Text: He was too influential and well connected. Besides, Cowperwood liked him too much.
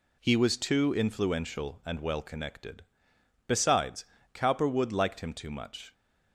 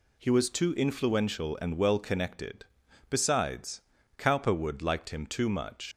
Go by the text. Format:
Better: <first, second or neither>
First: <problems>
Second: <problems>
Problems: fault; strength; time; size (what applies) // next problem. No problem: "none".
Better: first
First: none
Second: leaves "much" unfinished; at 5.9 s; 125 ms